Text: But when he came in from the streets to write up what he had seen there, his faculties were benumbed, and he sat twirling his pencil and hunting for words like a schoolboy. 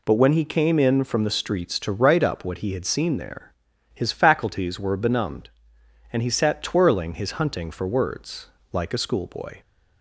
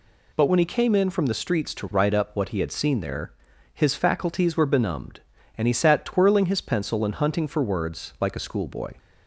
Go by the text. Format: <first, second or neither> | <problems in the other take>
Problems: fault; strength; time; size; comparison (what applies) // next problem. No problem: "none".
second | skips "pencil and"; at 7.3 s // pauses between "words" and "like"; slight; at 8.4 s; 0.25 s long